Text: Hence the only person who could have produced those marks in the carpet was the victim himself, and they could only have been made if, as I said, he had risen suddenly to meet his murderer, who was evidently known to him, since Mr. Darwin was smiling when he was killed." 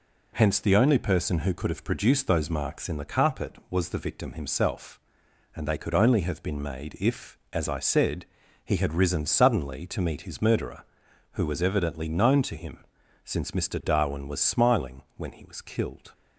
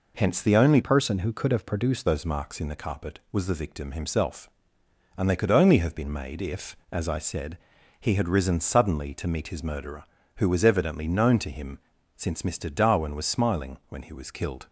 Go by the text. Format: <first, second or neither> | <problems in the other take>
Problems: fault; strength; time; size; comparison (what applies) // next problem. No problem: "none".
first | changes voice from "person" to "produced"; from 0.8 to 2.0 s; 1.2 s long